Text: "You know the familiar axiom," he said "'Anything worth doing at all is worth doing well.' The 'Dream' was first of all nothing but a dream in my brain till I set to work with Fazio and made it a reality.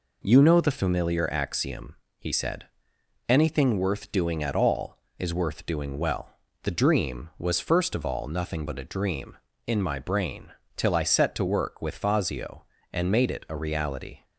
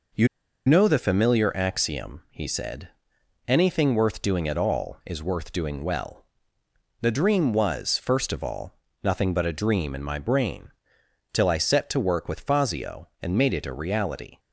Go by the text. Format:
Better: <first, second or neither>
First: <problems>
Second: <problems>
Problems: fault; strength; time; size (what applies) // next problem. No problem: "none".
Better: first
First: pauses between "said" and "Anything"; noticeable; at 2.6 s; 0.62 s long // pauses between "brain" and "till"; slight; at 10.5 s; 0.24 s long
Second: pauses between "You" and "know"; at 0.2 s; 0.39 s long // pauses between "said" and "Anything"; noticeable; at 2.8 s; 0.58 s long // pauses between "all" and "nothing"; slight; at 8.7 s; 0.24 s long // pauses between "brain" and "till"; noticeable; at 10.7 s; 0.60 s long